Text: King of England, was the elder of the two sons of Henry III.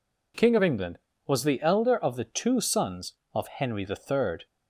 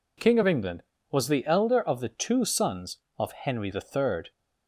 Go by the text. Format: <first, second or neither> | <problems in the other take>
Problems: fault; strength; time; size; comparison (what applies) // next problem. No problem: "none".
neither | none